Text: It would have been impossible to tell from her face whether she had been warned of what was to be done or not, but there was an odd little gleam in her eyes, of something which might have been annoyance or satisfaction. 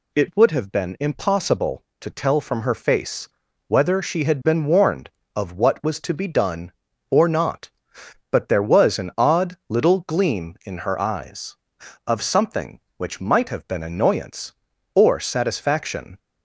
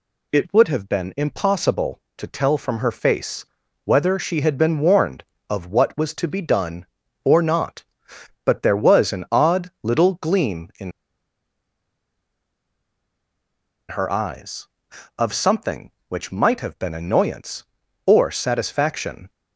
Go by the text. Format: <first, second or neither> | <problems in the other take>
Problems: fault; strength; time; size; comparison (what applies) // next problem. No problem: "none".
first | pauses between "face" and "whether"; at 3.4 s; 0.38 s long; also in the first // pauses between "in" and "her"; strong; at 10.9 s; 3.0 s long